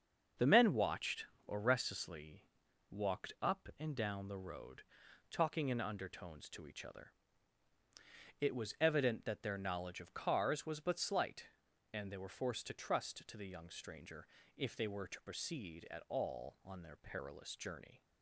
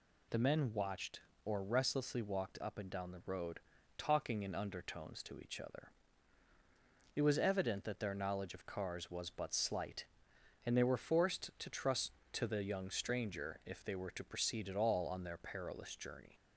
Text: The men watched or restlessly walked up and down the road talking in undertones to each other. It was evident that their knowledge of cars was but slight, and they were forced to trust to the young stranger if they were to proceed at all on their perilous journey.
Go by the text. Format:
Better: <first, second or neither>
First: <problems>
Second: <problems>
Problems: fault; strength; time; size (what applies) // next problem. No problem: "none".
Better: second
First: loses the start of "The"; at 0.3 s; 25 ms // starts louder than the rest; until 1.5 s; 7 dB // pauses between "restlessly" and "walked"; noticeable; at 2.4 s; 0.48 s long // pauses between "road" and "talking"; noticeable; at 4.8 s; 0.48 s long // pauses between "stranger" and "if"; slight; at 14.2 s; 0.30 s long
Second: pauses between "road" and "talking"; slight; at 3.6 s; 0.36 s long